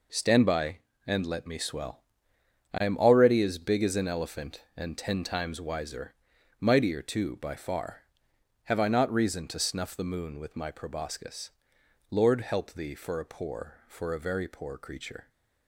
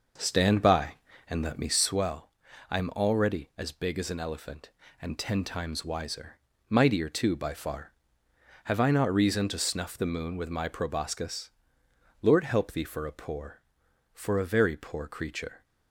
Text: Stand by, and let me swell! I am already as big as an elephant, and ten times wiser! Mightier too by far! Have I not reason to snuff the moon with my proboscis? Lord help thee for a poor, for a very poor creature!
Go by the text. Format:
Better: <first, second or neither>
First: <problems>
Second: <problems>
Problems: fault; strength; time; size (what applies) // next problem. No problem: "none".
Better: first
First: none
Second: starts louder than the rest; noticeable; until 2.0 s; 6 dB